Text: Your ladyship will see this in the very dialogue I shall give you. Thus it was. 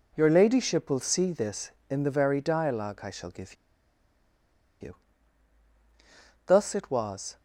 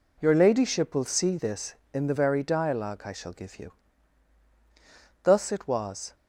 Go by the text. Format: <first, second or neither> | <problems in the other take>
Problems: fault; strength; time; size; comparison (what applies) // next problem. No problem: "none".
second | pauses between "give" and "you"; strong; at 3.5 s; 1.2 s long